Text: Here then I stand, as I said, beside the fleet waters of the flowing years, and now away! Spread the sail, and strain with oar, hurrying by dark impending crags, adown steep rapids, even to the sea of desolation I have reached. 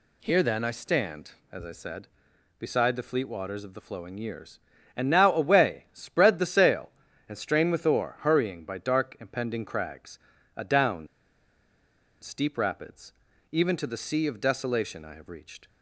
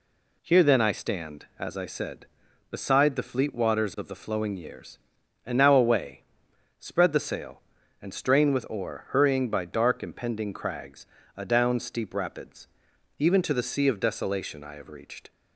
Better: second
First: pauses between "adown" and "steep"; at 11.0 s; 1.1 s long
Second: none

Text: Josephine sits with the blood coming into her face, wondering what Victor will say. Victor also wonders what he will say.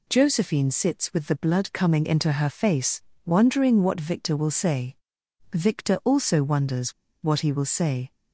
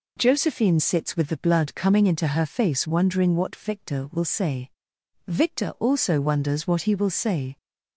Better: second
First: pauses between "wonders" and "what"; slight; at 6.9 s; 0.31 s long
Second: none

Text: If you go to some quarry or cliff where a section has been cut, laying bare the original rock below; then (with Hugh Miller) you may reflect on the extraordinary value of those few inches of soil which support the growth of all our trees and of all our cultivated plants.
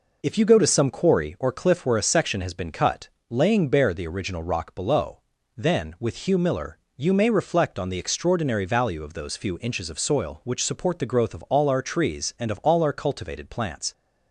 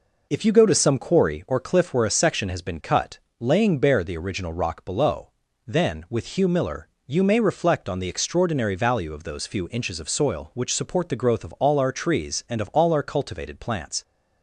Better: neither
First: none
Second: none

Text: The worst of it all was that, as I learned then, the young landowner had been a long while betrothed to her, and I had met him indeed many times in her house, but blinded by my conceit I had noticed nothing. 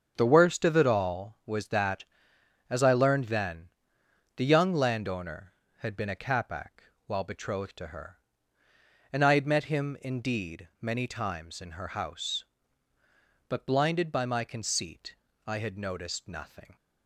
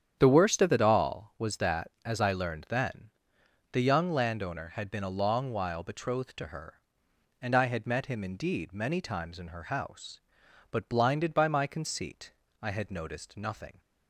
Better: second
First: starts louder than the rest; strong; until 1.1 s; 7.5 dB // says "capac" for "long"; at 6.1 s // pauses between "conceit" and "I"; slight; at 15.1 s; 0.32 s long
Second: starts louder than the rest; strong; until 1.2 s; 9 dB // pauses between "conceit" and "I"; slight; at 12.3 s; 0.28 s long

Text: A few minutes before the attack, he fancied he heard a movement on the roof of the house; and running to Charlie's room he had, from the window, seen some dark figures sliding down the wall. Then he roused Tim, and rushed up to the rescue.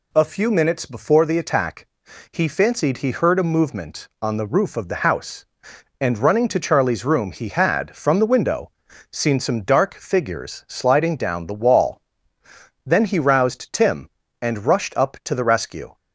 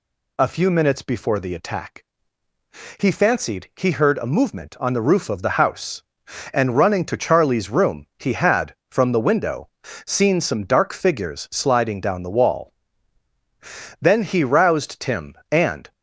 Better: first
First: none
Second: stops before "rushed up to the rescue"; at 15.9 s

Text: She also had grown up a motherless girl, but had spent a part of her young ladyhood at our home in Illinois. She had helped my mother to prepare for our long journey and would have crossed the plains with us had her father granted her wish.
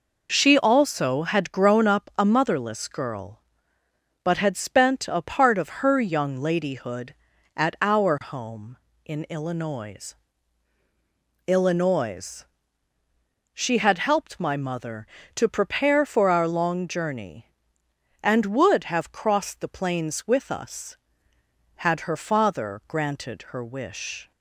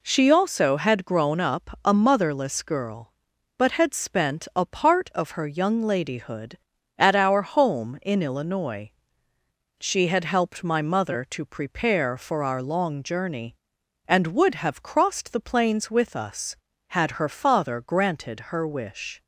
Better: second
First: says "Illinois" twice; at 11.4 s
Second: none

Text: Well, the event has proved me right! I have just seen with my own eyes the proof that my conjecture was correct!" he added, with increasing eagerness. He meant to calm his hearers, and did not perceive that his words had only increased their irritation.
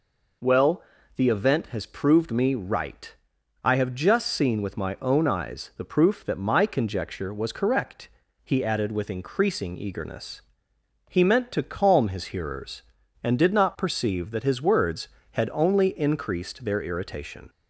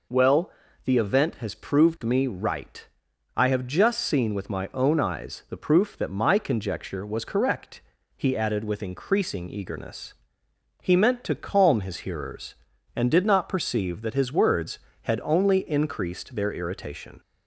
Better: neither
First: none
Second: none

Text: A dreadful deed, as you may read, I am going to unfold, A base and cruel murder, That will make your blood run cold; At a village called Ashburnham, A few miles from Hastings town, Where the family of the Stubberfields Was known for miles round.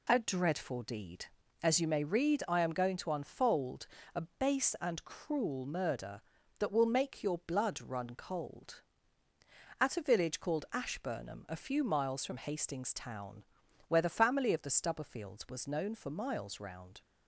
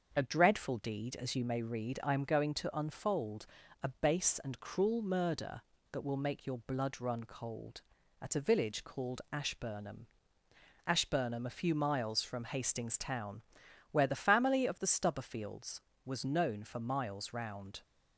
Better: first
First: none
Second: starts louder than the rest; until 1.1 s; 6.5 dB // says "Ashburnham" twice; at 10.8 s

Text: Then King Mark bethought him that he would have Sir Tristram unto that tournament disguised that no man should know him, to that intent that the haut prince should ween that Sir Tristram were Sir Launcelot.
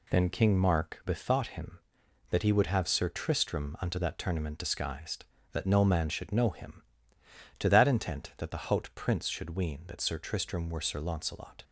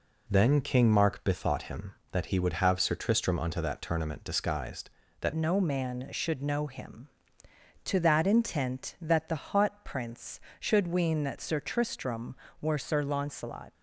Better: first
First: none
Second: changes voice at "no"; from 5.3 s on; 8.4 s long

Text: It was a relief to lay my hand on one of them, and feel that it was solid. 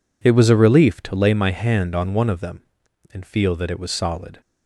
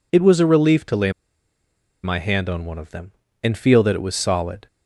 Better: first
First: none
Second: pauses between "lay" and "my"; noticeable; at 1.0 s; 0.93 s long

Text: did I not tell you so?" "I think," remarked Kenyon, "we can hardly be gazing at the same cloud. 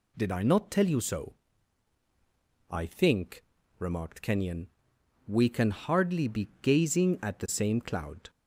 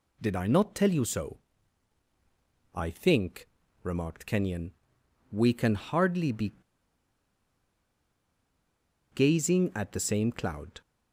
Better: first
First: none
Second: pauses between "be" and "gazing"; strong; at 6.5 s; 2.5 s long

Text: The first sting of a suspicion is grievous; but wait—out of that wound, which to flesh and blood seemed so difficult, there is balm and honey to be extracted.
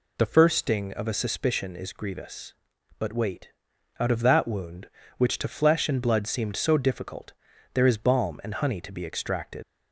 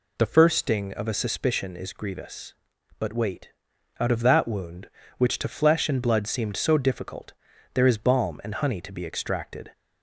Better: second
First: leaves "extracted" unfinished; at 9.6 s; 90 ms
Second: none

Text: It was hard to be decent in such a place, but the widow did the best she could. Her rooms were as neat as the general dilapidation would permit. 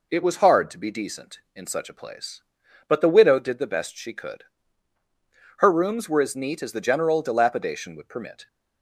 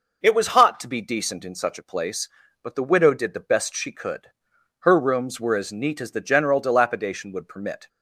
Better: first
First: none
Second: says "hot" for "hard"; at 0.4 s

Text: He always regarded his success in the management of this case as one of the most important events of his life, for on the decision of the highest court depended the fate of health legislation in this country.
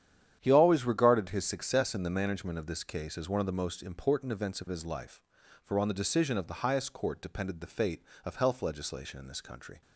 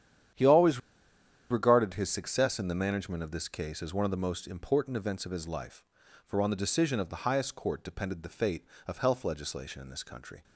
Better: first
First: starts louder than the rest; strong; until 1.4 s; 10 dB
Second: starts louder than the rest; strong; until 2.0 s; 10 dB // pauses between "always" and "regarded"; noticeable; at 0.7 s; 0.71 s long

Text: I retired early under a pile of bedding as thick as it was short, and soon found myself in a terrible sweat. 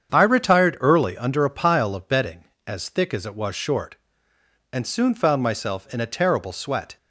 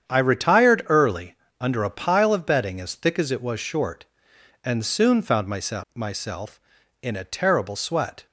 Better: first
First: starts louder than the rest; strong; until 1.1 s; 8 dB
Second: starts louder than the rest; strong; until 1.1 s; 8.5 dB // pauses between "early" and "under"; slight; at 1.3 s; 0.26 s long // says "myself" twice; at 5.9 s

